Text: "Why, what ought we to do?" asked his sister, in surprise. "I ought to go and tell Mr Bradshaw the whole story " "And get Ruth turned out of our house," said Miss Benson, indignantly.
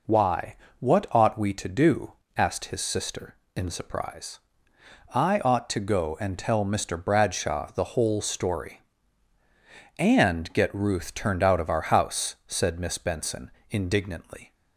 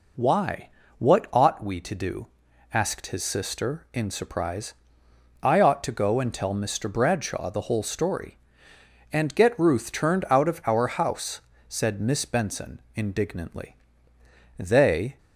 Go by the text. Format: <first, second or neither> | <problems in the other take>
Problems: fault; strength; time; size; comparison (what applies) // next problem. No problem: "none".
first | goes on to say "They"; noticeable; from 14.5 s on; 0.62 s long